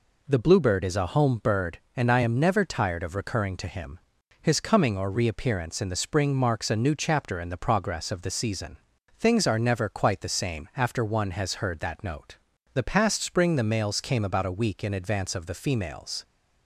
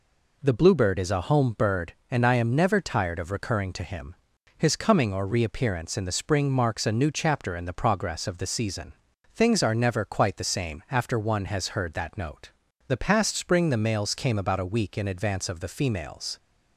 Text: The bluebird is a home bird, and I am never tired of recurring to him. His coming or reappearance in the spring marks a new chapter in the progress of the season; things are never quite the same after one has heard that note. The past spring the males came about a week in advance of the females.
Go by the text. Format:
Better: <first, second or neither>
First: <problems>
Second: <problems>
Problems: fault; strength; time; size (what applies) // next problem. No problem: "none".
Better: neither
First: none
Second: none